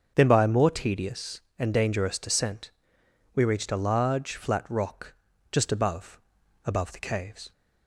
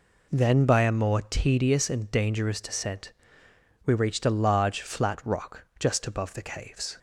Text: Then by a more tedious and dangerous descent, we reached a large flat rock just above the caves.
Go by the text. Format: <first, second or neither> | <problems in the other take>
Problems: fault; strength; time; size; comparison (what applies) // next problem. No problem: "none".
second | starts louder than the rest; until 1.1 s; 7 dB // pauses between "rock" and "just"; at 5.1 s; 0.38 s long // says "above" twice; at 6.6 s